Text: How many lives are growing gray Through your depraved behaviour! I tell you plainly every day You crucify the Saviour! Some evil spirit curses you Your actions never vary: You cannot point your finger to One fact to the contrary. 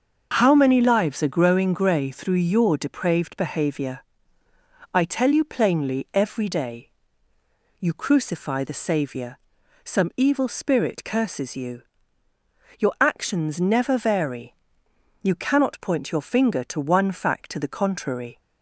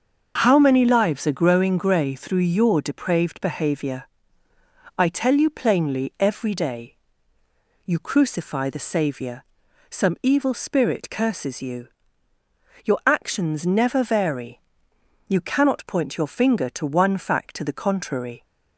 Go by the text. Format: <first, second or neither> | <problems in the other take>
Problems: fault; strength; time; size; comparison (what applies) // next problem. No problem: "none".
neither | pauses between "day" and "You"; noticeable; the same in both // pauses between "you" and "Your"; noticeable; the same in both